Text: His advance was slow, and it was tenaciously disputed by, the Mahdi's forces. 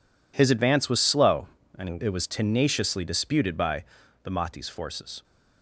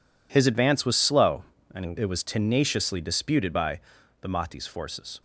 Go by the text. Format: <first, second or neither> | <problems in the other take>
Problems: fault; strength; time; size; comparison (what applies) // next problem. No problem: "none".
neither | none